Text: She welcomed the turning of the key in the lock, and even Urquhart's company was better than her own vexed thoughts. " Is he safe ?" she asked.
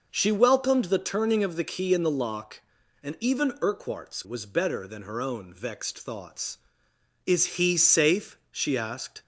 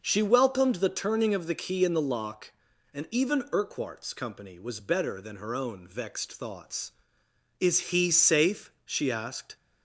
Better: second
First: skips "company"; at 4.2 s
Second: none

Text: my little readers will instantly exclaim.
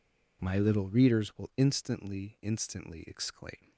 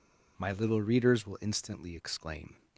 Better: second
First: says "instantly" twice; at 2.4 s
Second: none

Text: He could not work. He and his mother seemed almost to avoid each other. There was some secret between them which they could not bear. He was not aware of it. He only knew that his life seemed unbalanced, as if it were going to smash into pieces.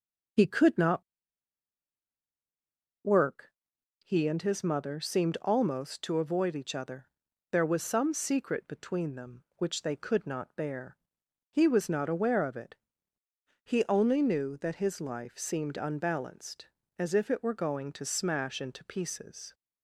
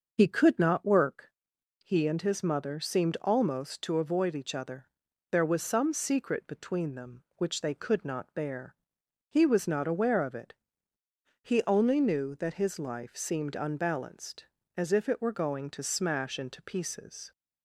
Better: second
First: starts louder than the rest; until 3.3 s; 6 dB // pauses between "not" and "work"; strong; at 1.0 s; 2.0 s long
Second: starts louder than the rest; until 1.1 s; 6 dB

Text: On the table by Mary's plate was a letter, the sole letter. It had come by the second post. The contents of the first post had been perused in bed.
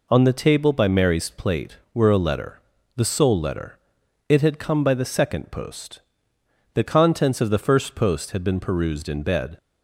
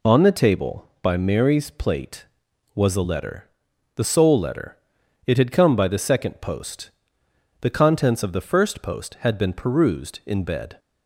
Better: second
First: says "were" for "was"; at 1.9 s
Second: none

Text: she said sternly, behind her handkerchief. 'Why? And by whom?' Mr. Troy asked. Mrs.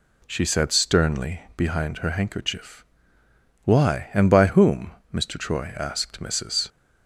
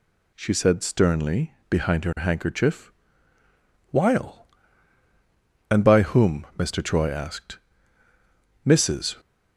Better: first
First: none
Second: says "While" for "Why"; at 3.8 s

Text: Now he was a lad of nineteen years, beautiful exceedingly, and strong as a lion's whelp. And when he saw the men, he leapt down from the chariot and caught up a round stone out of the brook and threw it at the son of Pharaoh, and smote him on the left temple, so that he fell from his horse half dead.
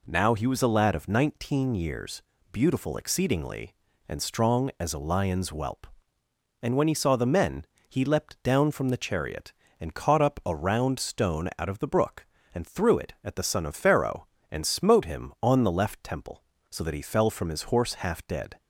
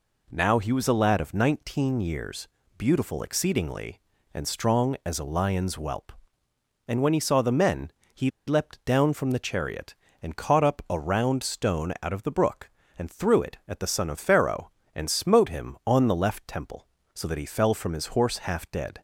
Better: first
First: none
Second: pauses between "he" and "leapt"; slight; at 8.2 s; 0.18 s long

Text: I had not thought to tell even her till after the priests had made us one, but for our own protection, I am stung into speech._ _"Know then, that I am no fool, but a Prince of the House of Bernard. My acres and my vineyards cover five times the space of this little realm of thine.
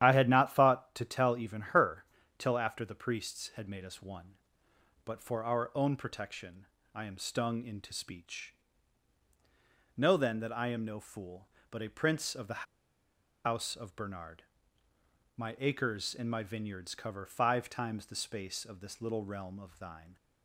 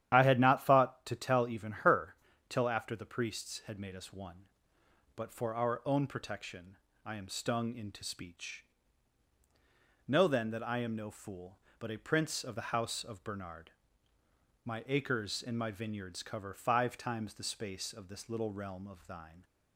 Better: second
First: starts louder than the rest; strong; until 1.0 s; 11 dB // pauses between "her" and "till"; slight; at 2.0 s; 0.34 s long // pauses between "the" and "House"; noticeable; at 12.6 s; 0.80 s long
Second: starts louder than the rest; strong; until 1.1 s; 11 dB // pauses between "her" and "till"; slight; at 2.1 s; 0.34 s long

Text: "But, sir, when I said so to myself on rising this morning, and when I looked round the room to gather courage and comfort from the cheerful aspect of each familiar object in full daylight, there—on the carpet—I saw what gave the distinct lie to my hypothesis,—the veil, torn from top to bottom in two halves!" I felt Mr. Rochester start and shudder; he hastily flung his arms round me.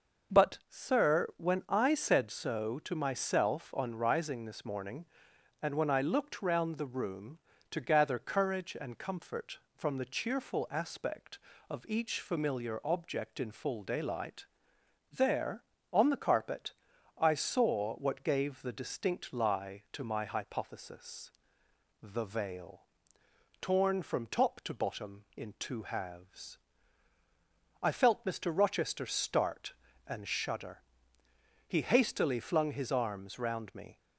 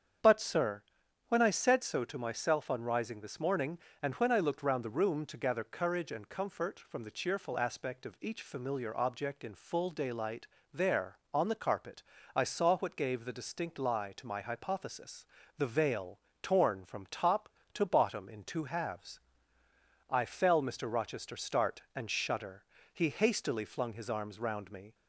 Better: first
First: none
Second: starts louder than the rest; strong; until 1.6 s; 8 dB // says "fell" for "felt"; at 20.2 s

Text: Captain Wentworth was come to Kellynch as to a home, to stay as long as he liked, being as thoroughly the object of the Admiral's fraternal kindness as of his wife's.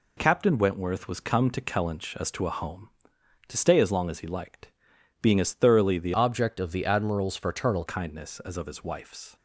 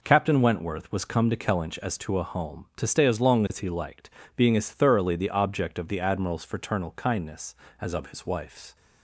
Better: second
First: changes voice from "object" to "fraternal"; from 6.1 to 7.8 s; 1.7 s long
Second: none

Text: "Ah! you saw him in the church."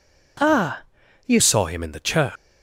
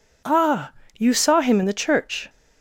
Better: second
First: changes voice at "saw"; from 1.3 s on; 0.9 s long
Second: none

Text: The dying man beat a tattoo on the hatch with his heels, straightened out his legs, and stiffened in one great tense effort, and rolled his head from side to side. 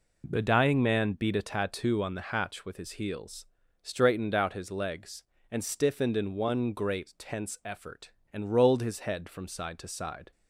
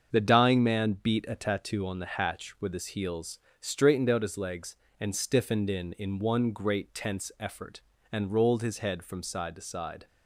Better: first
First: none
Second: starts louder than the rest; until 1.1 s; 7 dB // says "in" twice; at 5.9 s

